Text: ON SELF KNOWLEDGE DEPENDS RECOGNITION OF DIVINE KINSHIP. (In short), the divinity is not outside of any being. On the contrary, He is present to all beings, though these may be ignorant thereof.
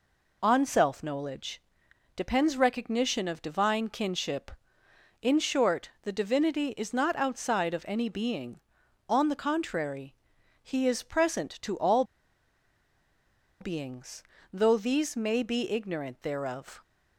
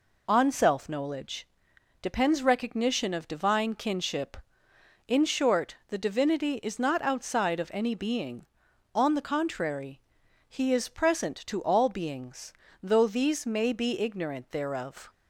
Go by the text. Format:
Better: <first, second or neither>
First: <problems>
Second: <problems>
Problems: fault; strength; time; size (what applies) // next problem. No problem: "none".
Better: second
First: pauses between "KNOWLEDGE" and "DEPENDS"; noticeable; at 1.6 s; 0.56 s long // pauses between "all" and "beings"; strong; at 12.0 s; 1.5 s long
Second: pauses between "KNOWLEDGE" and "DEPENDS"; noticeable; at 1.4 s; 0.56 s long